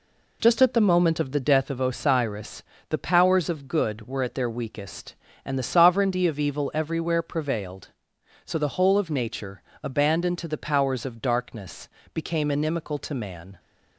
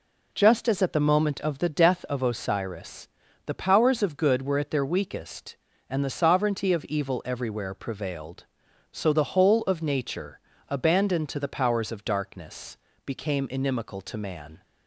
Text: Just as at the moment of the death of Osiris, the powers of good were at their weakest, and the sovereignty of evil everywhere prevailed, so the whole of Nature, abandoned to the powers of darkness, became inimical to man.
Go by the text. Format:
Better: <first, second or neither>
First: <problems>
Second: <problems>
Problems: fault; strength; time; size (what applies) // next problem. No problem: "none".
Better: second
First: skips "as"; at 0.6 s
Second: none